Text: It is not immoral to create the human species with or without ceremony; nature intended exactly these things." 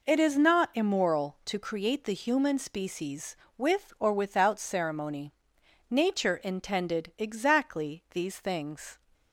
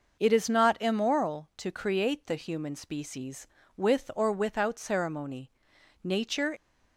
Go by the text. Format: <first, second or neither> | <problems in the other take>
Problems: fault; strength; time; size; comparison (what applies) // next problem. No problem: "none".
first | stops before "intended exactly these things"; at 6.5 s